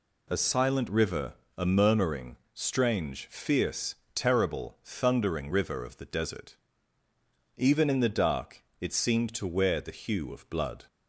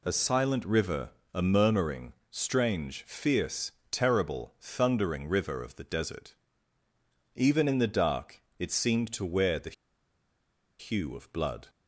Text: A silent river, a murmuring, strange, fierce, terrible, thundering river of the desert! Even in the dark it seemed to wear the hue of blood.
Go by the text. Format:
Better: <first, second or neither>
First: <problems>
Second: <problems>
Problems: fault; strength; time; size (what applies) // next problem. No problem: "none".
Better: first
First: pauses between "dark" and "it"; slight; at 8.6 s; 0.16 s long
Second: pauses between "dark" and "it"; slight; at 8.4 s; 0.16 s long // pauses between "the" and "hue"; at 9.7 s; 1.0 s long